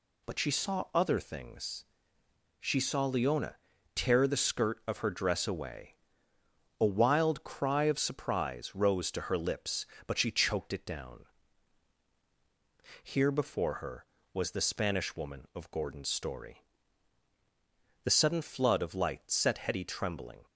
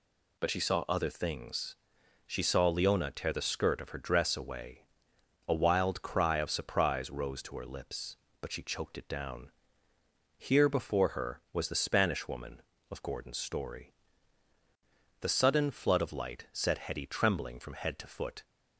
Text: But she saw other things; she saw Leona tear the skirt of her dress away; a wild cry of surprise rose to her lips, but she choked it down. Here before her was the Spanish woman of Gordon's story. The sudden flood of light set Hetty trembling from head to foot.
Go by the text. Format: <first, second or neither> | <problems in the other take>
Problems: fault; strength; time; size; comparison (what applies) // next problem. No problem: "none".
second | pauses between "Leona" and "tear"; slight; at 3.5 s; 0.36 s long // stops before "from head to foot"; at 20.4 s